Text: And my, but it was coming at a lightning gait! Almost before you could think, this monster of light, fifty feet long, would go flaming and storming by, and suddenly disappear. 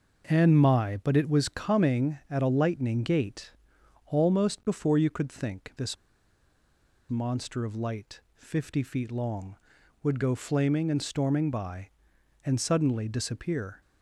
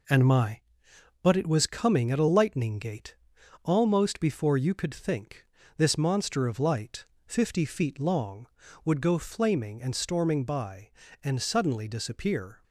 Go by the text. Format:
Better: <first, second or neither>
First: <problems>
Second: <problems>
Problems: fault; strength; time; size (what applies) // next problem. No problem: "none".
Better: second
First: pauses between "this" and "monster"; at 5.9 s; 1.1 s long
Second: none